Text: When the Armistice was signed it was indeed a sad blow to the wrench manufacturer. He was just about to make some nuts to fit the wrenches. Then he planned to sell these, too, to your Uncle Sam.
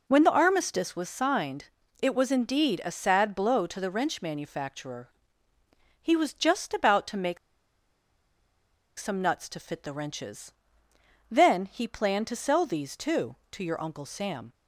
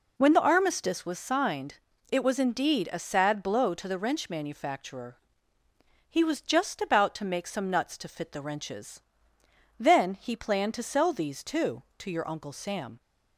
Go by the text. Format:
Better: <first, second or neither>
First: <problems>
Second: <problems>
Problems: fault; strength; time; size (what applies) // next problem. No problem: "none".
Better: second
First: pauses between "signed" and "it"; slight; at 1.6 s; 0.36 s long // pauses between "make" and "some"; strong; at 7.3 s; 1.6 s long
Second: pauses between "signed" and "it"; slight; at 1.7 s; 0.36 s long